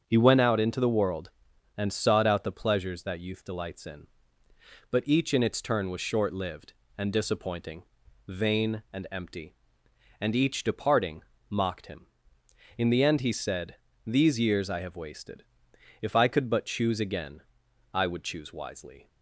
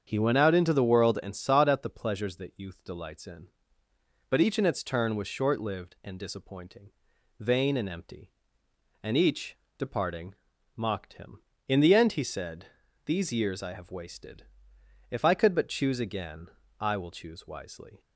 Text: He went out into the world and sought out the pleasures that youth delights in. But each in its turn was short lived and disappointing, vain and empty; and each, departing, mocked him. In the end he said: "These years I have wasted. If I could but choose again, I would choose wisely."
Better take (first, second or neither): first